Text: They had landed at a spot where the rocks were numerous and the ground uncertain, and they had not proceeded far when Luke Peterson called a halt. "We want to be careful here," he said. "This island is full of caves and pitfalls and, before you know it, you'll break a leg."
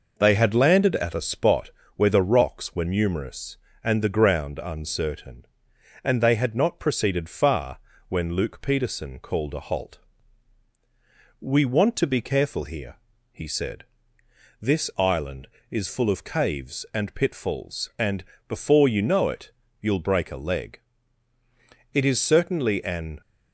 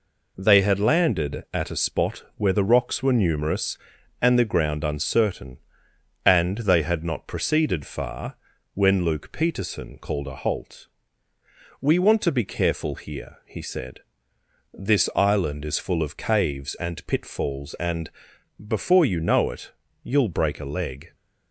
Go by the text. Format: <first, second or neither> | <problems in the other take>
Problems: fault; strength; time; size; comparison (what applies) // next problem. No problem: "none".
second | pauses between "spot" and "where"; slight; at 1.6 s; 0.26 s long // pauses between "far" and "when"; slight; at 7.7 s; 0.30 s long; also in the second // goes on to say "It is certainly an"; noticeable; from 21.9 s on; 1.2 s long